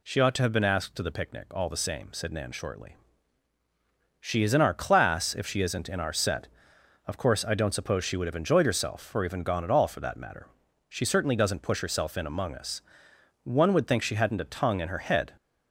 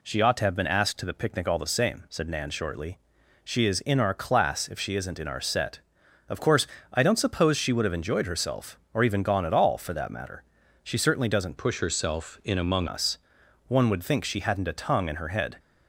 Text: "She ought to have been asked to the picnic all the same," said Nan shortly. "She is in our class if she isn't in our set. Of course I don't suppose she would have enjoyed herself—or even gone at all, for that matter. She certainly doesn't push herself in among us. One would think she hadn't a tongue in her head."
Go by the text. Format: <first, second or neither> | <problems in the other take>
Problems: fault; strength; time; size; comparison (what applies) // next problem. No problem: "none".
first | pauses between "course" and "I"; slight; at 6.6 s; 0.24 s long // changes voice from "push" to "among"; from 11.5 to 12.8 s; 1.3 s long